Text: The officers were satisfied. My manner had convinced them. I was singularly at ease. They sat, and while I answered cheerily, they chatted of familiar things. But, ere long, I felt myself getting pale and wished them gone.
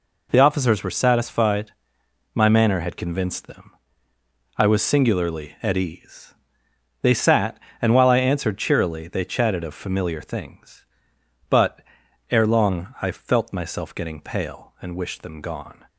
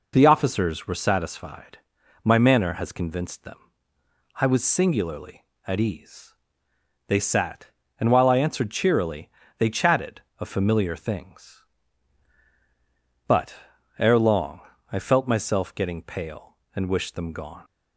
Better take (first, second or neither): first